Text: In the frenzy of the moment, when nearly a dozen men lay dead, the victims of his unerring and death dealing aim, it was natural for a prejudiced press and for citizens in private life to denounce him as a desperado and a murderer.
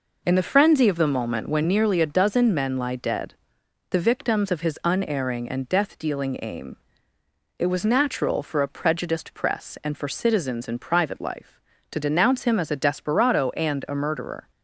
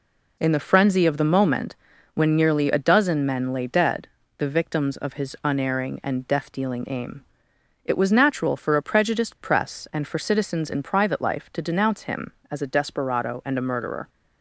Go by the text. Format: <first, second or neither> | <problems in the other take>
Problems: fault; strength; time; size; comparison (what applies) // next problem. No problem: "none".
second | says "lie" for "lay"; at 2.7 s